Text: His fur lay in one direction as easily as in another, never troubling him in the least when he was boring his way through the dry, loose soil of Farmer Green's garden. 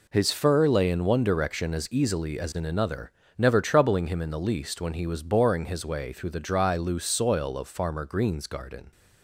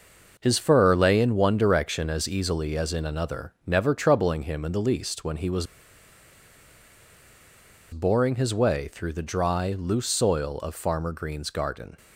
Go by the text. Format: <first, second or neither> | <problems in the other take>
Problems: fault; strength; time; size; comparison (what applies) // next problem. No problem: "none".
first | pauses between "was" and "boring"; strong; at 5.6 s; 2.2 s long